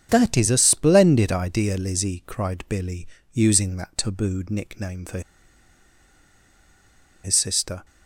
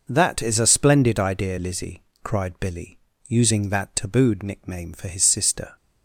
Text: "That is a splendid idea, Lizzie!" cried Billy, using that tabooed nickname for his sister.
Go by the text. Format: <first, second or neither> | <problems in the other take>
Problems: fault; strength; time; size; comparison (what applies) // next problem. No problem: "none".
second | starts louder than the rest; strong; until 1.1 s; 7.5 dB // pauses between "for" and "his"; strong; at 5.2 s; 2.0 s long